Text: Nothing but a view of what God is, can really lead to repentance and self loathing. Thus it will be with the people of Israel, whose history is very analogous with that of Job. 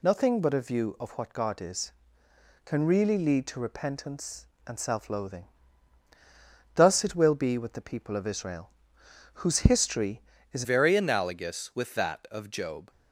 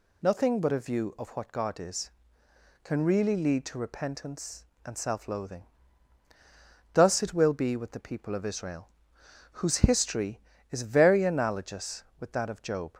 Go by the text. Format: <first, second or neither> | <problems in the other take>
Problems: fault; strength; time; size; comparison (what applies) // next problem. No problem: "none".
second | changes voice at "very"; from 10.6 s on; 2.2 s long